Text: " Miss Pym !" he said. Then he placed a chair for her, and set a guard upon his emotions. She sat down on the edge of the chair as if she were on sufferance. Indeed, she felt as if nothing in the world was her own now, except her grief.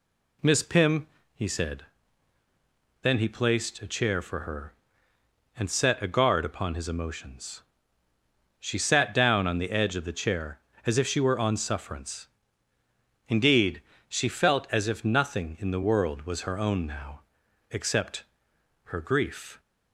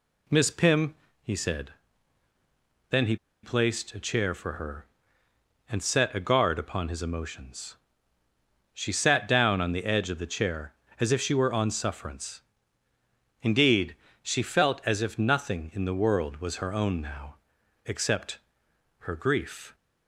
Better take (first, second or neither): first